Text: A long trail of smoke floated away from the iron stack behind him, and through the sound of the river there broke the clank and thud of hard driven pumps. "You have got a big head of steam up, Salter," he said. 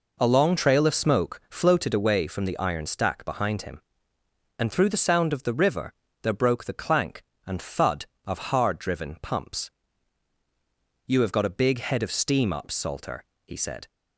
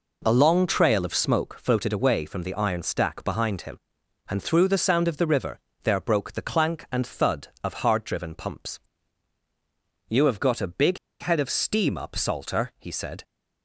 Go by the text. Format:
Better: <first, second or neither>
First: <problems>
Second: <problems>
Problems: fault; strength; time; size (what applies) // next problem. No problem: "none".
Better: first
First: pauses between "river" and "there"; slight; at 5.9 s; 0.30 s long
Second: pauses between "river" and "there"; slight; at 5.5 s; 0.24 s long // pauses between "big" and "head"; slight; at 10.9 s; 0.23 s long